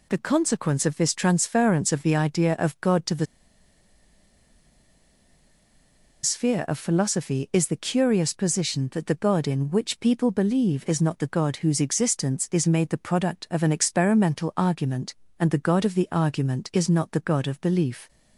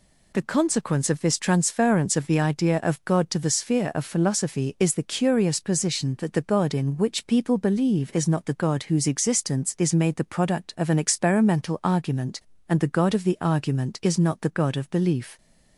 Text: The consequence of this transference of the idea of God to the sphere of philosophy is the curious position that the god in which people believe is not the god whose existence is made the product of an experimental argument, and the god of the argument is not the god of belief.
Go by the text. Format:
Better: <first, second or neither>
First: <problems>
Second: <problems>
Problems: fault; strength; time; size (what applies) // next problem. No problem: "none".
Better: second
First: pauses between "the" and "sphere"; strong; at 3.2 s; 2.9 s long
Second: none